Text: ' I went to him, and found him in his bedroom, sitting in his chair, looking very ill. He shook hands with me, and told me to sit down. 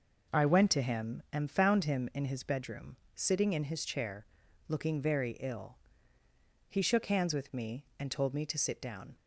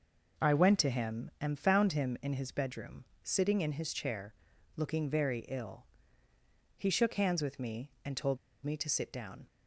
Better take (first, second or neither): first